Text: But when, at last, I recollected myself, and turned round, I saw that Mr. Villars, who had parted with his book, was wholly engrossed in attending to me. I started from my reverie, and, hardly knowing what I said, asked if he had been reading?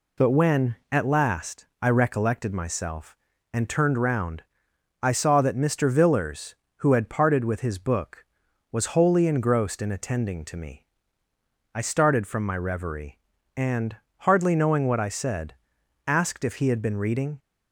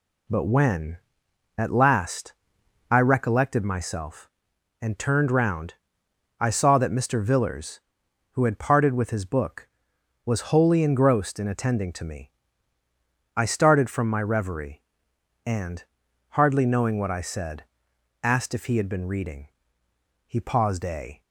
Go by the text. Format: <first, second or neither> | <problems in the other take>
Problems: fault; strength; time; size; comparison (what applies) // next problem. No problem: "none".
first | goes on to say "He paused a"; noticeable; from 20.2 s on; 0.94 s long